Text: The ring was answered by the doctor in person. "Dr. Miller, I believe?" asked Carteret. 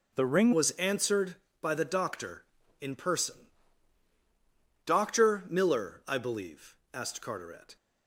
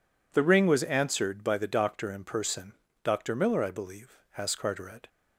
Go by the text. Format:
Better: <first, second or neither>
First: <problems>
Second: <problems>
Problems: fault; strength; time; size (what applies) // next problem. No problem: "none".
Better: second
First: changes voice at "was"; from 0.5 s on; 7.2 s long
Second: none